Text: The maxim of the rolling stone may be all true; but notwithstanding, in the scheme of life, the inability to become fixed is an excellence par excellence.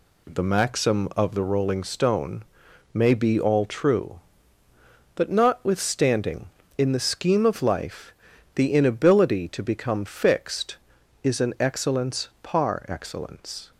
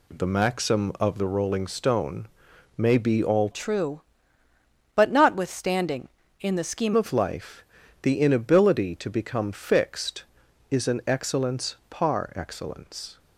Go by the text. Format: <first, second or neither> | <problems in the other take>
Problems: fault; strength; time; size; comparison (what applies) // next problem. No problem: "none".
first | pauses between "stone" and "may"; noticeable; at 2.2 s; 0.50 s long; noticeable in the first // changes voice from "true" to "scheme"; from 3.5 to 6.9 s; 3.4 s long // pauses between "excellence" and "par"; slight; at 11.7 s; 0.16 s long; slight in the first